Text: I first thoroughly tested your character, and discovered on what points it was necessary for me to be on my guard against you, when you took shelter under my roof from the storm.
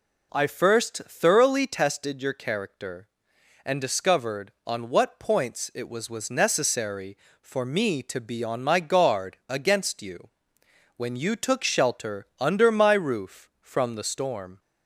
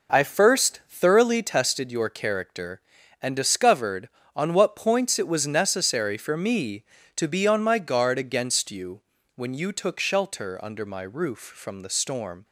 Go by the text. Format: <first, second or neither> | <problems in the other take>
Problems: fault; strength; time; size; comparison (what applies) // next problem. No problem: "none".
second | says "was" twice; at 6.0 s